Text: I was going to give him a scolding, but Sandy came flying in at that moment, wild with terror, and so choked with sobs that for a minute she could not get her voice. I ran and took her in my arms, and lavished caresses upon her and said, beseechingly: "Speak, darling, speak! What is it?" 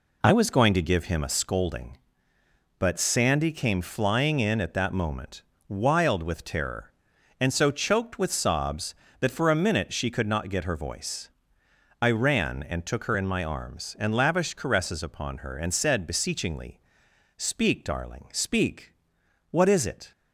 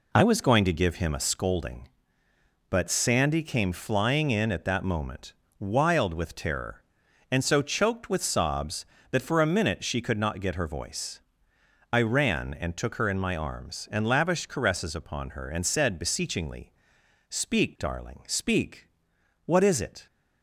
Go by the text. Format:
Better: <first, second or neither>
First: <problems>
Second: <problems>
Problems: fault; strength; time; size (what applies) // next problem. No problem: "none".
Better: neither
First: none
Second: none